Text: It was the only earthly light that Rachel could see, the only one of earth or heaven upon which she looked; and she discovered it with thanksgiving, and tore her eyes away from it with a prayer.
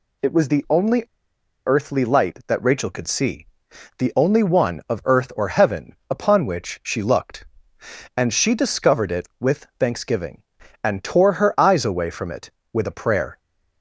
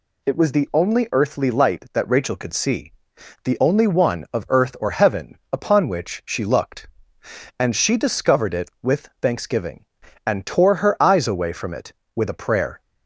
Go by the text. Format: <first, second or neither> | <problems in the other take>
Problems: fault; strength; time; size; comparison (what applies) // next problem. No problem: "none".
second | pauses between "only" and "earthly"; noticeable; at 1.0 s; 0.60 s long // pauses between "heaven" and "upon"; slight; at 5.9 s; 0.16 s long; slight in the second